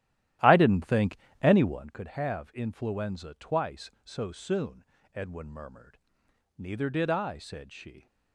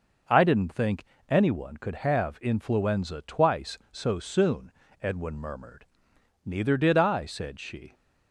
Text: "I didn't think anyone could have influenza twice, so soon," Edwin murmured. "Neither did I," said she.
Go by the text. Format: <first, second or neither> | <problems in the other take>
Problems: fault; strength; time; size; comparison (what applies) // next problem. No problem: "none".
second | starts louder than the rest; strong; until 2.0 s; 13.5 dB // pauses between "think" and "anyone"; slight; at 1.1 s; 0.24 s long; slight in the second